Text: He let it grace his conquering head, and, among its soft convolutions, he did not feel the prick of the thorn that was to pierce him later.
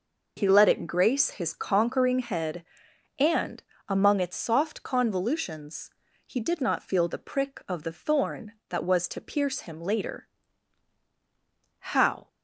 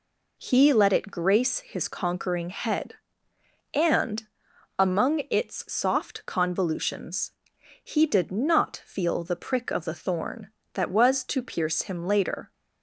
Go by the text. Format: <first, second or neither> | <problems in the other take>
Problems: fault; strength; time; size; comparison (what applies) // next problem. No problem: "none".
second | goes on to say "How"; slight; from 11.7 s on; 0.48 s long